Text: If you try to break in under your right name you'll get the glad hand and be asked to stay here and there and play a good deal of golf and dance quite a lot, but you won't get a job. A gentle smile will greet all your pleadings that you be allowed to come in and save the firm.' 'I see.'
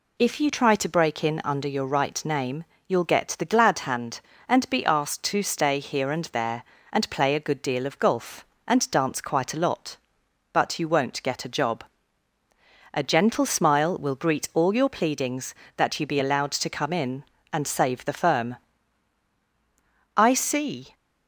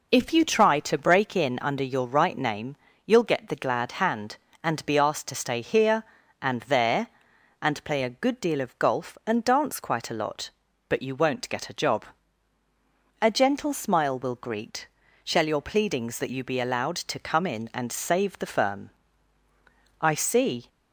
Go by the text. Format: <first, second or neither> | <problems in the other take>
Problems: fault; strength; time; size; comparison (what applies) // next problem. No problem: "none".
first | pauses between "name" and "you'll"; slight; at 2.7 s; 0.30 s long; slight in the first // says "shall" for "all"; at 15.2 s